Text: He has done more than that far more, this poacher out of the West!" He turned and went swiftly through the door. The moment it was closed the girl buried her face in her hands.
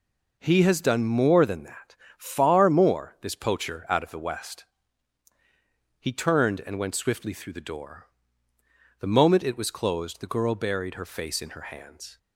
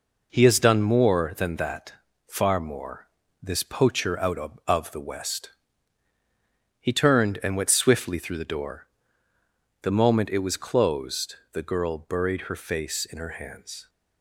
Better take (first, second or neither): first